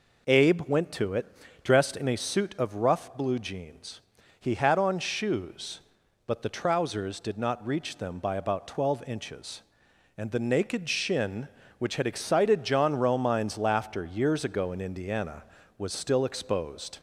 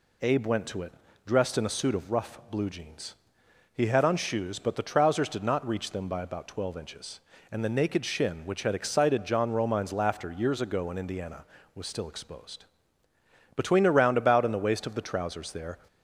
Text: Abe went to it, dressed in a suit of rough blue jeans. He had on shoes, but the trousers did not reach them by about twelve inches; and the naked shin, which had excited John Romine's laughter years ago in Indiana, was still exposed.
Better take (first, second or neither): first